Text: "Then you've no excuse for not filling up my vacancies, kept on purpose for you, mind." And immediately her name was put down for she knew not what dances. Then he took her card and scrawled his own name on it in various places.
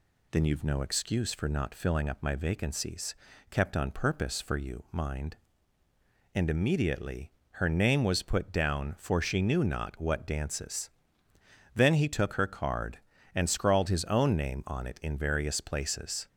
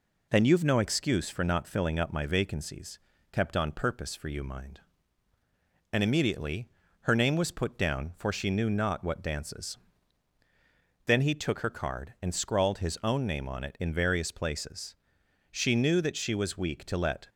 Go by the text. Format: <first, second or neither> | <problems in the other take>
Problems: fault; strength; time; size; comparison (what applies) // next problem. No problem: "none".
first | pauses between "immediately" and "her"; slight; at 6.6 s; 0.32 s long; slight in the first // goes on to say "She knew that she was weak to let"; strong; from 15.5 s on; 1.7 s long